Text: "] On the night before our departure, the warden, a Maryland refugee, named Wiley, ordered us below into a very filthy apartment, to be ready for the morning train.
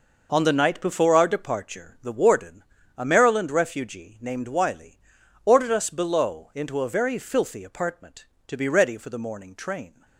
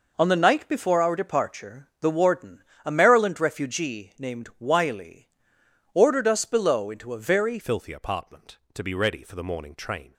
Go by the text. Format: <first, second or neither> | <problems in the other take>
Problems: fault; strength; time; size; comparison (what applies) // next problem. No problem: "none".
first | changes voice at "filthy"; from 7.5 s on; 2.6 s long